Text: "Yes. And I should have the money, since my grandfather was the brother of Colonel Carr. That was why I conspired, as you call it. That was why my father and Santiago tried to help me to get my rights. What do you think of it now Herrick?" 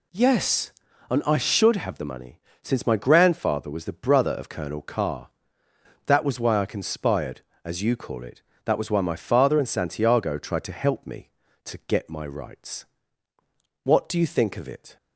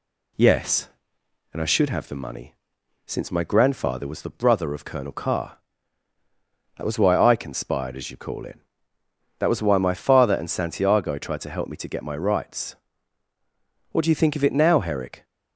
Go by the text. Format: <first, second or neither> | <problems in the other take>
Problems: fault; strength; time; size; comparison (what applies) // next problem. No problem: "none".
second | stops before "now Herrick"; at 14.9 s